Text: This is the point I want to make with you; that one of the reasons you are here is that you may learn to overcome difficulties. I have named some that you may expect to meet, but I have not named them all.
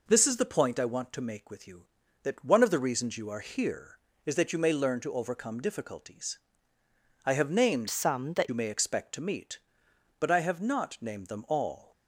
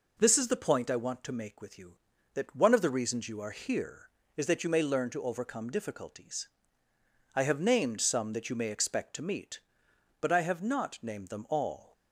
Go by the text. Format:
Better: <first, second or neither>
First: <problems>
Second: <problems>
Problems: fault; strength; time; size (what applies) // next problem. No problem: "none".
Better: second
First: changes voice from "some" to "that"; from 7.8 to 8.4 s; 0.6 s long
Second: none